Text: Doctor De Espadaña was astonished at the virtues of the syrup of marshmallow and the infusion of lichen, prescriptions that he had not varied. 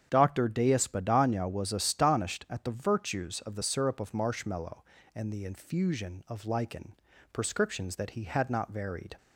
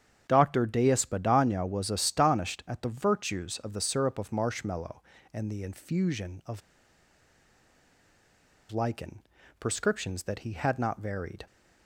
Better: first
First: starts louder than the rest; strong; until 1.1 s; 8 dB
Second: starts louder than the rest; strong; until 1.3 s; 8 dB // pauses between "of" and "lichen"; strong; at 6.6 s; 2.1 s long

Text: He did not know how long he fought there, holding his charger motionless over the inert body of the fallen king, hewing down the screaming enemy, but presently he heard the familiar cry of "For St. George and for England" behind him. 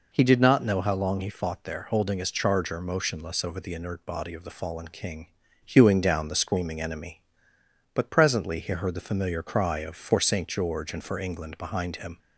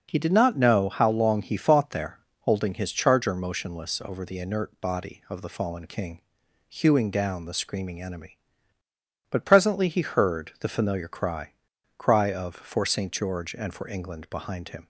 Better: first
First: none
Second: says "cry" twice; at 11.9 s

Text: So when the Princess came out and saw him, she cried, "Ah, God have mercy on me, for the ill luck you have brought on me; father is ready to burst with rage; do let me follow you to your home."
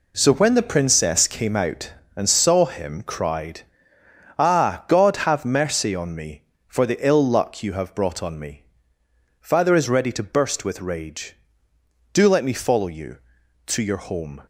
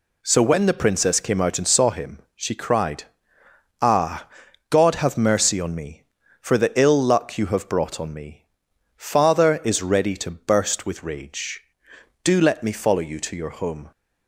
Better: second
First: skips "she"; at 3.0 s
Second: none

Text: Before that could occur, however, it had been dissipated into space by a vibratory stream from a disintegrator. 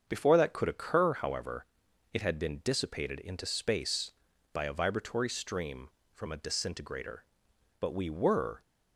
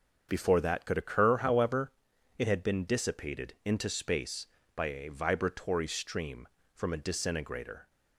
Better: second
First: starts louder than the rest; until 1.0 s; 7 dB // goes on to say "But we were"; noticeable; from 7.7 s on; 0.82 s long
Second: starts louder than the rest; until 1.3 s; 7 dB

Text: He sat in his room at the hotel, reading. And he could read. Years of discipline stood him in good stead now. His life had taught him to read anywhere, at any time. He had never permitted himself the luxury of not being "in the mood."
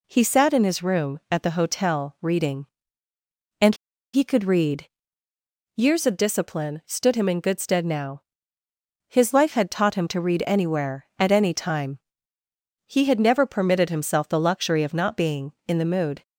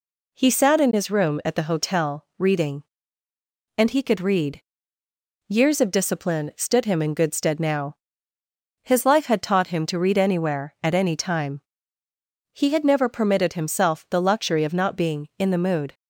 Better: second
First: pauses between "And" and "he"; at 3.7 s; 0.39 s long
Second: none

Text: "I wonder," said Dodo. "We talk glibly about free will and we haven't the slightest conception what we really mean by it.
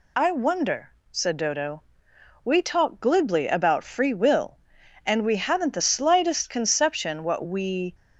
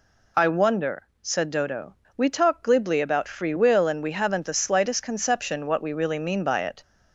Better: second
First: stops before "really mean by it"; at 7.9 s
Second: none

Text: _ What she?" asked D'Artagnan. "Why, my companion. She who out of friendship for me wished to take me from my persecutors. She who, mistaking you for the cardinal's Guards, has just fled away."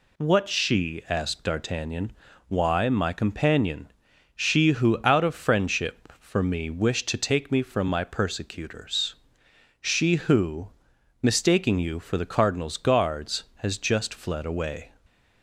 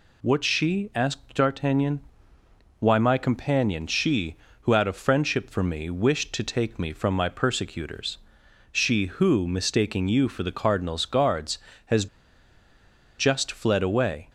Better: first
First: none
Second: pauses between "has" and "just"; at 12.0 s; 1.1 s long

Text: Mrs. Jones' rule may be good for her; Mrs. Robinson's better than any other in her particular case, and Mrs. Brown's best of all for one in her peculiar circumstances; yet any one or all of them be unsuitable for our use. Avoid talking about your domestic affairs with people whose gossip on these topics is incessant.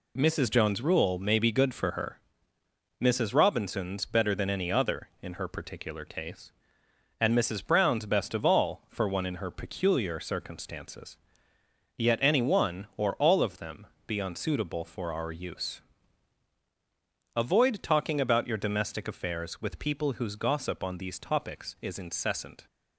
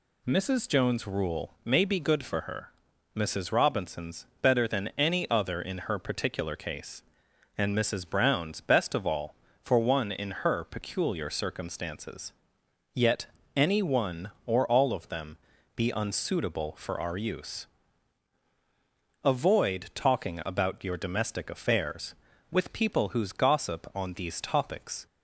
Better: first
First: pauses between "them" and "be"; slight; at 13.8 s; 0.20 s long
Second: pauses between "yet" and "any"; slight; at 13.2 s; 0.28 s long // pauses between "them" and "be"; at 15.3 s; 0.40 s long // stops before "is incessant"; at 25.0 s

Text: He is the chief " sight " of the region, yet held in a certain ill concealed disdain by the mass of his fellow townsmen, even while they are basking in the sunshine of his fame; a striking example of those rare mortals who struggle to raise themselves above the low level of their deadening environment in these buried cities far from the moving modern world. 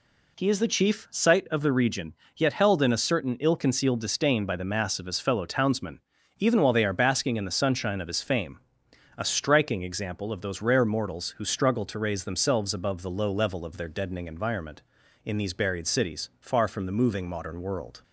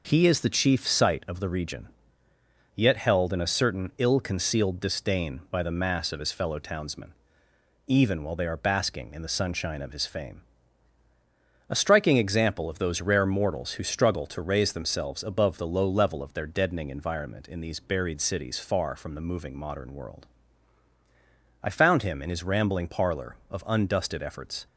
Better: first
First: none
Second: goes on to say "I found him in his rambling parlor of undusted efforts"; strong; from 21.6 s on; 3.0 s long

